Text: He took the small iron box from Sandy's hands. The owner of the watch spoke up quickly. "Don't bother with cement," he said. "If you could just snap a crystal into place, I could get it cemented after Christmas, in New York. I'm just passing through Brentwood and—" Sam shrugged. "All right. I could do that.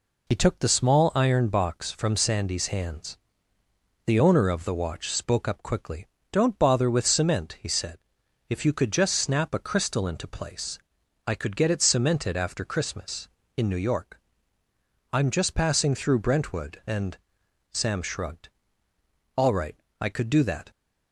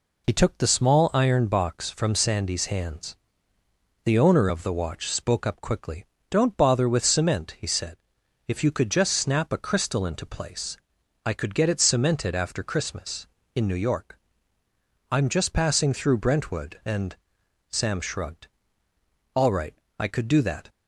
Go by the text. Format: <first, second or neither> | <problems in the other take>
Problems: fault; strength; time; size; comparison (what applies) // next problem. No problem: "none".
neither | none